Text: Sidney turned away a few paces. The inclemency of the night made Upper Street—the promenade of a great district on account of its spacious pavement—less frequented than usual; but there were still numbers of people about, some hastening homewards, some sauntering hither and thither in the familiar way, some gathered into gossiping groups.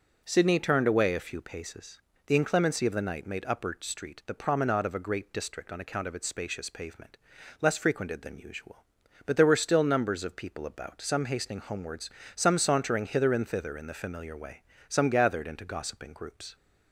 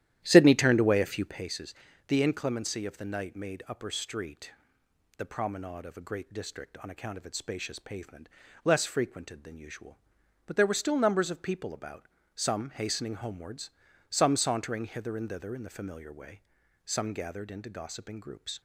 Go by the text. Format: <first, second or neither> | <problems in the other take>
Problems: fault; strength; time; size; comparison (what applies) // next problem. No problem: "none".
first | starts louder than the rest; strong; until 1.4 s; 12 dB